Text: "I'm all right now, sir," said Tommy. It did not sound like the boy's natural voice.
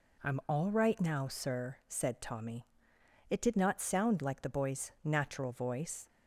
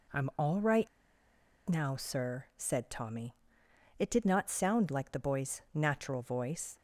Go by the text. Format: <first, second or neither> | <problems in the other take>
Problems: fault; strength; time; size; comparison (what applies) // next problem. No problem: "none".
first | pauses between "right" and "now"; noticeable; at 0.8 s; 0.79 s long